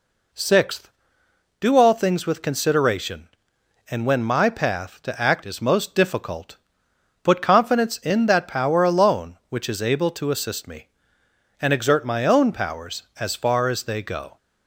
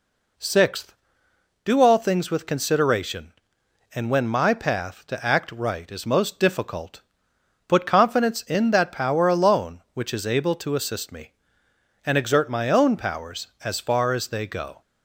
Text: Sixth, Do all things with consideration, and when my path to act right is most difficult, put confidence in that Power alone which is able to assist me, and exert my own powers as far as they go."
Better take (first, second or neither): second